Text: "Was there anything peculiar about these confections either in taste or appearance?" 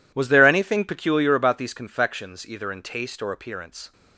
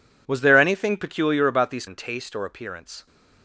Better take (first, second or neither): first